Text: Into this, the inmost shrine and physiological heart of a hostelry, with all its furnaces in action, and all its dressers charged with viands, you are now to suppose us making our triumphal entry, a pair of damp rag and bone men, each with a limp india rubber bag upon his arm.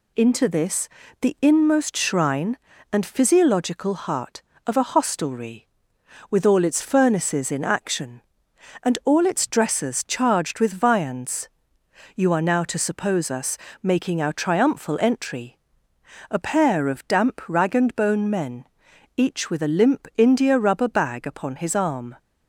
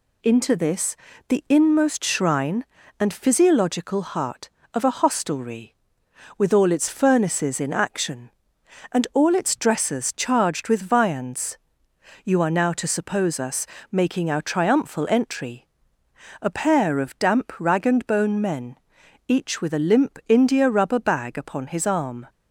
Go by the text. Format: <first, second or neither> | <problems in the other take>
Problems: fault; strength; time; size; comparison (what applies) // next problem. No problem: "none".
neither | pauses between "us" and "making"; slight; the same in both